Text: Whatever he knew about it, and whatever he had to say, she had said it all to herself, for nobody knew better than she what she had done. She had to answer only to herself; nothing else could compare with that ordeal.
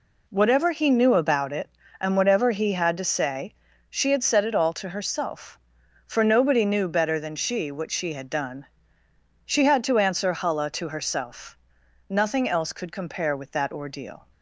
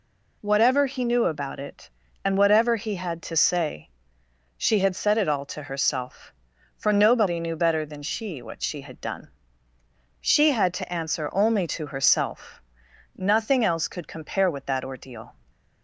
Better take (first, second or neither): second